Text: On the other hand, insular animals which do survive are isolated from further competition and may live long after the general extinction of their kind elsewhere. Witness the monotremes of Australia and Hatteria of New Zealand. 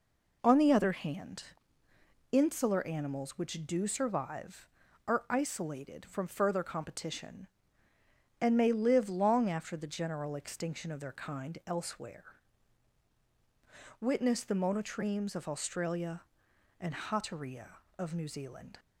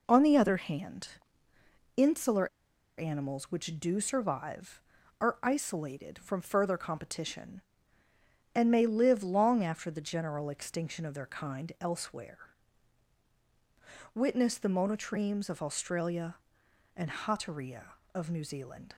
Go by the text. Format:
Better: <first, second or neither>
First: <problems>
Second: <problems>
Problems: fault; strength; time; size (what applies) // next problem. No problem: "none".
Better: first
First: none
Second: pauses between "insular" and "animals"; noticeable; at 2.4 s; 0.52 s long